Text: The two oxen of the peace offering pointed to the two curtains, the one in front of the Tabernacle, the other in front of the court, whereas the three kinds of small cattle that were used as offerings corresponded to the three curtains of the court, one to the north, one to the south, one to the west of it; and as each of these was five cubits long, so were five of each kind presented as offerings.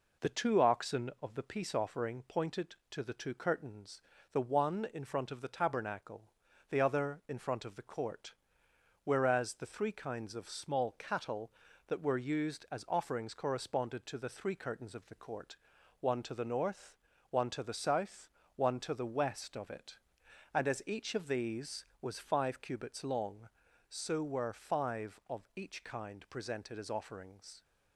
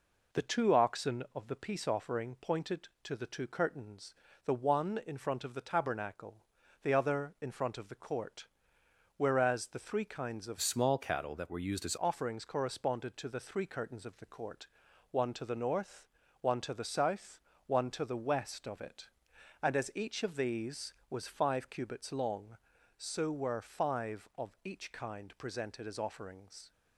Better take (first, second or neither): first